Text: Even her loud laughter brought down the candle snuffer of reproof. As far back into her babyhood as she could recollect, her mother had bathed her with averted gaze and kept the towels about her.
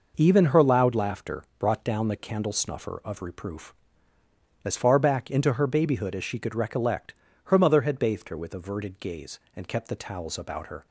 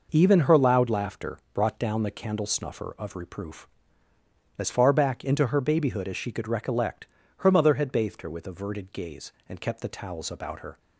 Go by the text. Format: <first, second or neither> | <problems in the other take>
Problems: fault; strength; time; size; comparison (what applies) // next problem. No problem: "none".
neither | pauses between "laughter" and "brought"; slight; the same in both